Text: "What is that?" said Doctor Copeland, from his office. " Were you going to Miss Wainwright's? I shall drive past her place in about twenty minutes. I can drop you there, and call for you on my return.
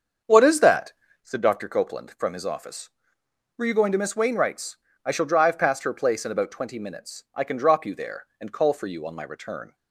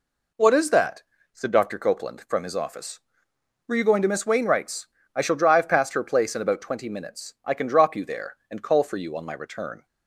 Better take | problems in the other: second | starts louder than the rest; until 1.3 s; 7 dB

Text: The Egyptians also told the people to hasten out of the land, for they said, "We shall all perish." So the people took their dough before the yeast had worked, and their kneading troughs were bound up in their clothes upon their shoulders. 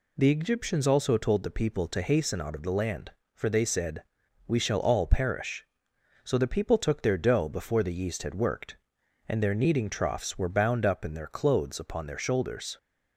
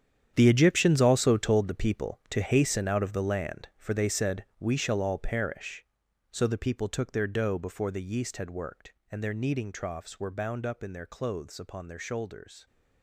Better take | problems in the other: first | gets quieter; strong; throughout; 13.5 dB

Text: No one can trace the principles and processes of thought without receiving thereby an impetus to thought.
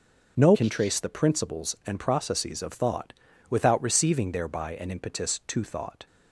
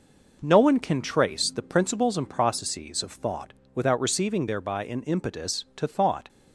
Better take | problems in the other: second | skips "one"; at 0.5 s // pauses between "thought" and "without"; at 3.1 s; 0.38 s long; slight in the second

